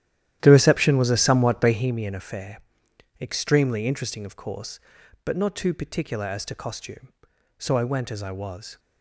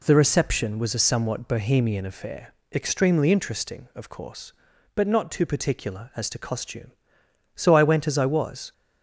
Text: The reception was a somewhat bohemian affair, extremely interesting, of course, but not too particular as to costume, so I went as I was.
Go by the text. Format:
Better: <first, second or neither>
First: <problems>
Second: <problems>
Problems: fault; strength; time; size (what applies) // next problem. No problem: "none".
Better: second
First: starts louder than the rest; strong; until 1.9 s; 12 dB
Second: none